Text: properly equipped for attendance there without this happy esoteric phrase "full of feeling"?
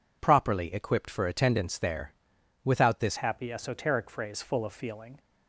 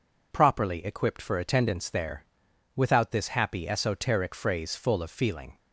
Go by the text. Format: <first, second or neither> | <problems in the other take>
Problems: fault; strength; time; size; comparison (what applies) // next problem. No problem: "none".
second | pauses between "there" and "without"; noticeable; at 2.1 s; 0.52 s long; noticeable in the second // changes voice at "happy"; from 3.1 s on; 2.0 s long